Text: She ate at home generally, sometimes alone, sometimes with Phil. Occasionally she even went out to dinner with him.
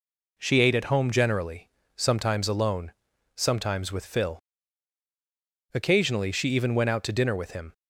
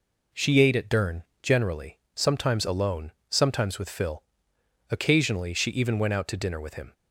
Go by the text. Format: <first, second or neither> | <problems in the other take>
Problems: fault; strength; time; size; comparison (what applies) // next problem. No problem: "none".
first | says "dern" for "home"; at 0.8 s